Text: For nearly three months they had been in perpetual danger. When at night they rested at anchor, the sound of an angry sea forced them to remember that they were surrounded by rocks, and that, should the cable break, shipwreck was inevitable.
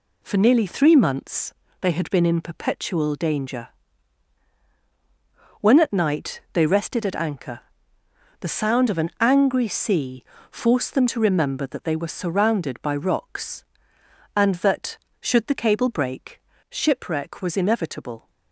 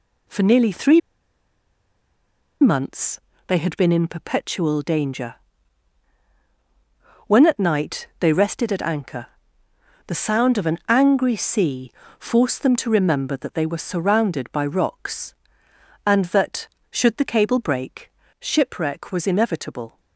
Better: first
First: pauses between "months" and "they"; slight; at 1.5 s; 0.28 s long // pauses between "sea" and "forced"; slight; at 10.2 s; 0.26 s long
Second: pauses between "three" and "months"; strong; at 1.0 s; 1.6 s long // pauses between "months" and "they"; slight; at 3.1 s; 0.28 s long // pauses between "sea" and "forced"; slight; at 11.9 s; 0.26 s long

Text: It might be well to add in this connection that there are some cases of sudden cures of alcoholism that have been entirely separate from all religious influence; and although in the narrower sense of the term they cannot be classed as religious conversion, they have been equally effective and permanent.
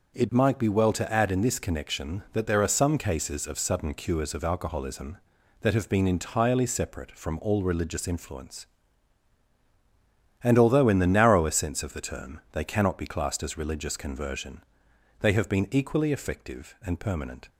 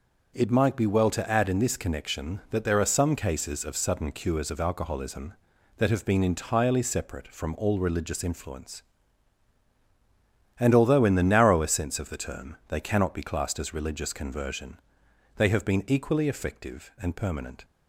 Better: neither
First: none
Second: none

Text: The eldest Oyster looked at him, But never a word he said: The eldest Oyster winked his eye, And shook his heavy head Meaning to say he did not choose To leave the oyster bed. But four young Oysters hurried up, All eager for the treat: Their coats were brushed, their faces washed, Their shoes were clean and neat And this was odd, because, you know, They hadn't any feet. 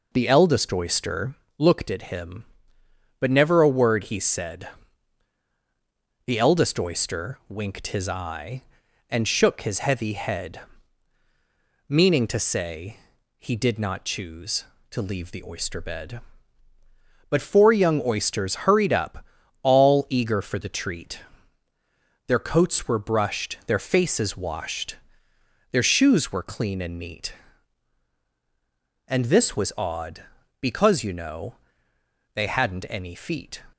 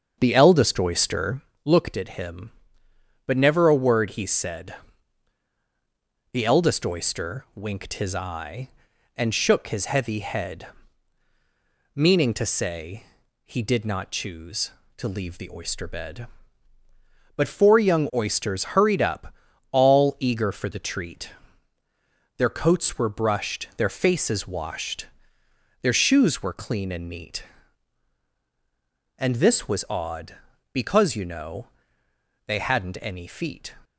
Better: first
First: pauses between "Oyster" and "looked"; slight; at 1.3 s; 0.22 s long // pauses between "head" and "Meaning"; strong; at 10.5 s; 1.2 s long // pauses between "say" and "he"; at 12.9 s; 0.42 s long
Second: starts louder than the rest; until 1.5 s; 7 dB // pauses between "Oyster" and "looked"; slight; at 1.4 s; 0.22 s long // pauses between "head" and "Meaning"; strong; at 10.6 s; 1.2 s long // pauses between "say" and "he"; at 13.0 s; 0.42 s long

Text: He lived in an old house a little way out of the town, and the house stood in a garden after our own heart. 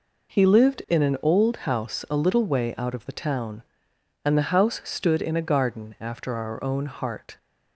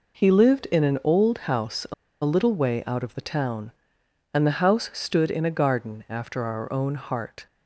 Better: first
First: none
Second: pauses between "a" and "little"; slight; at 1.9 s; 0.30 s long

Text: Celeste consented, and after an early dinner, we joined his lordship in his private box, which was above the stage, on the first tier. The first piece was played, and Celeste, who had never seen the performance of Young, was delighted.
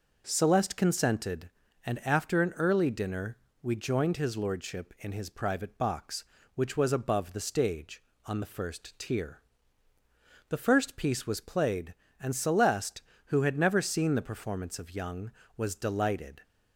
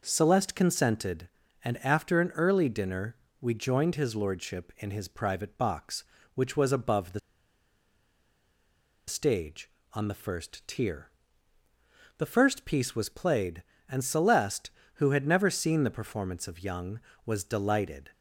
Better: first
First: none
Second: pauses between "the" and "stage"; strong; at 7.1 s; 1.8 s long

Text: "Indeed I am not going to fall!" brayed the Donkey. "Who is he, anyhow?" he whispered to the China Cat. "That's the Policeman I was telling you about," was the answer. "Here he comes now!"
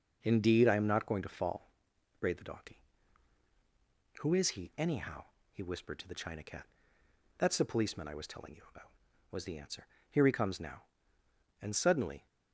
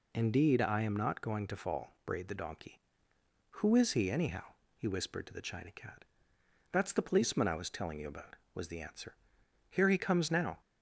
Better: second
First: goes on to say "And suddenly"; noticeable; from 11.6 s on; 0.64 s long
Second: none

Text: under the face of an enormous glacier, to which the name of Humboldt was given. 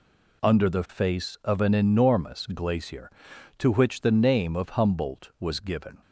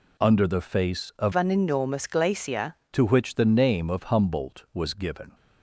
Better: first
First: none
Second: changes voice from "an" to "glacier"; from 1.3 to 2.7 s; 1.4 s long

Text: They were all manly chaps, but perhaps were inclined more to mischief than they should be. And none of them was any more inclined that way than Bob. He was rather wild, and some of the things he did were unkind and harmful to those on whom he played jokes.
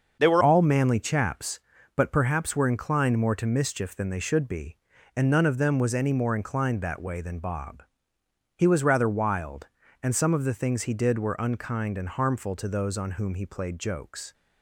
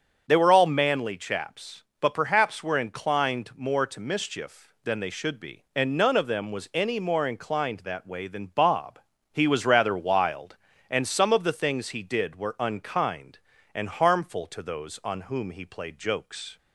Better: second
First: starts louder than the rest; until 1.2 s; 6.5 dB // changes voice at "all"; from 0.4 s on; 13.9 s long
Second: starts louder than the rest; until 1.2 s; 7 dB

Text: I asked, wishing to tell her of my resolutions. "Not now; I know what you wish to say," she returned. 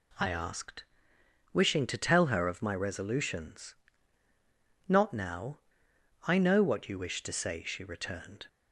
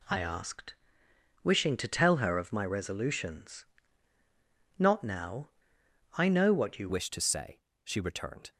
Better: first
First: none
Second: changes voice at "wish"; from 6.8 s on; 1.7 s long

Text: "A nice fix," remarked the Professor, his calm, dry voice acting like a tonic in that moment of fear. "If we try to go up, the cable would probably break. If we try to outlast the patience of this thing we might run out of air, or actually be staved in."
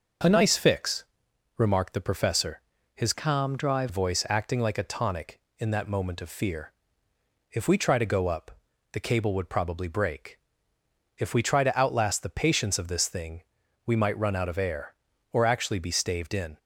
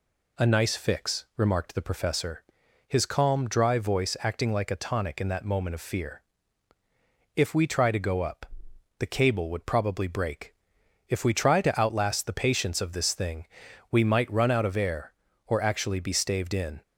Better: second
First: starts louder than the rest; until 1.8 s; 6.5 dB // changes voice from "calm" to "dry"; from 3.1 to 3.8 s; 0.7 s long // pauses between "thing" and "we"; at 13.4 s; 0.42 s long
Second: pauses between "thing" and "we"; at 13.4 s; 0.44 s long

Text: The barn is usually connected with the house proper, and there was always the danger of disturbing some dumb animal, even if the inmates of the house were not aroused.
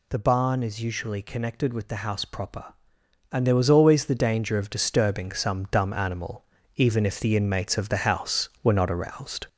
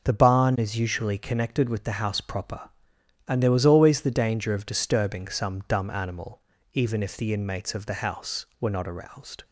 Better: second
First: gets louder; throughout; 4 dB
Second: none

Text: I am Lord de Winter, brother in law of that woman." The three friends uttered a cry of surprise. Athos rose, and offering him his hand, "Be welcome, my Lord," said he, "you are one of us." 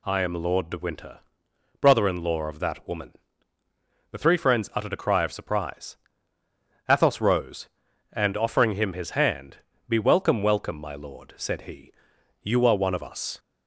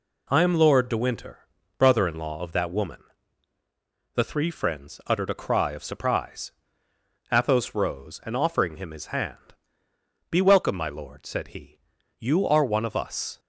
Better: second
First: says "welcome" twice; at 10.4 s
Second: none

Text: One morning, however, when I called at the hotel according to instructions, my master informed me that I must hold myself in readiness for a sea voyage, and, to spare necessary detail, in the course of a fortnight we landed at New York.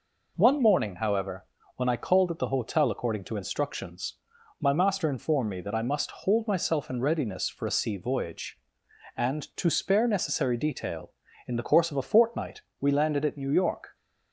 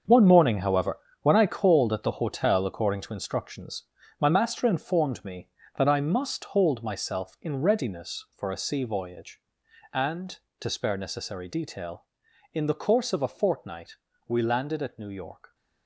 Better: first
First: pauses between "fortnight" and "we"; slight; at 12.6 s; 0.20 s long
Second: gets quieter; strong; throughout; 11.5 dB // pauses between "fortnight" and "we"; slight; at 13.9 s; 0.32 s long

